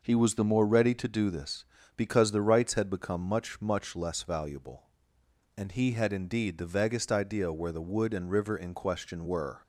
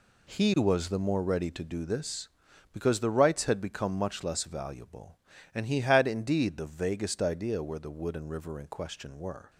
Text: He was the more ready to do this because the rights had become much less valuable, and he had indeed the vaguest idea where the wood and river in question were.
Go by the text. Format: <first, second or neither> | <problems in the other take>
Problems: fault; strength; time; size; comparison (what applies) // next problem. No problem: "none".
second | says "much" twice; at 3.6 s